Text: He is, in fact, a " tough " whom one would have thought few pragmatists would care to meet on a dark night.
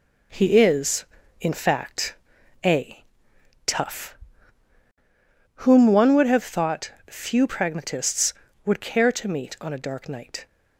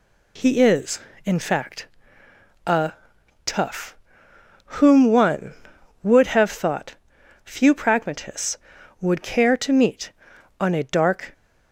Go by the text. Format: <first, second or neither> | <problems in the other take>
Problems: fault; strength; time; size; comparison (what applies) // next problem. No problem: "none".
first | pauses between "thought" and "few"; noticeable; at 6.9 s; 0.48 s long; slight in the first // stops before "night"; at 11.3 s